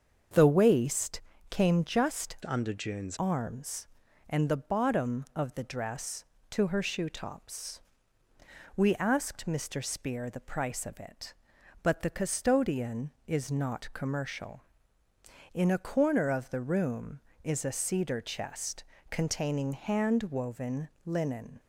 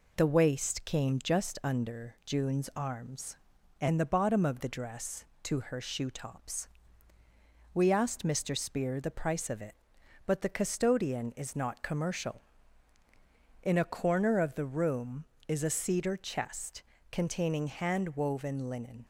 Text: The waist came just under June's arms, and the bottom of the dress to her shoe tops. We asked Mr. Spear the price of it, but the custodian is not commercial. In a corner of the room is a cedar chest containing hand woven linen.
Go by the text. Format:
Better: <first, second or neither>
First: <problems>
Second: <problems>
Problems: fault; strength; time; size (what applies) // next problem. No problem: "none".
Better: second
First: starts louder than the rest; until 1.6 s; 7 dB // pauses between "waist" and "came"; slight; at 1.2 s; 0.30 s long // changes voice from "under" to "June's"; from 2.4 to 3.1 s; 0.7 s long // pauses between "chest" and "containing"; slight; at 18.8 s; 0.26 s long // pauses between "woven" and "linen"; slight; at 20.8 s; 0.16 s long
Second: pauses between "chest" and "containing"; slight; at 16.8 s; 0.28 s long